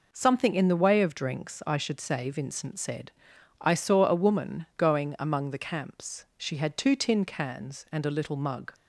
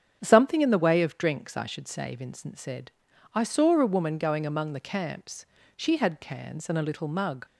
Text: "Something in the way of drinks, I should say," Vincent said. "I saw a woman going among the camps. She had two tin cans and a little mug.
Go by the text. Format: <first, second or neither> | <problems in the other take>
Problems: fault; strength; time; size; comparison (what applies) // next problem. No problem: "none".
first | starts louder than the rest; strong; until 1.2 s; 9 dB // skips "two tin"; at 6.2 s